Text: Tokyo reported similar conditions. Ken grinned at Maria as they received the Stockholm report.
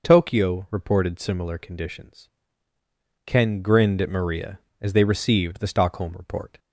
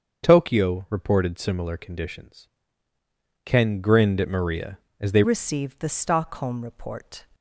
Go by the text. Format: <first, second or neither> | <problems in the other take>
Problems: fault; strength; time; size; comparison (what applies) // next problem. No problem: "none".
first | starts louder than the rest; until 1.2 s; 7 dB // changes voice at "received"; from 5.2 s on; 2.0 s long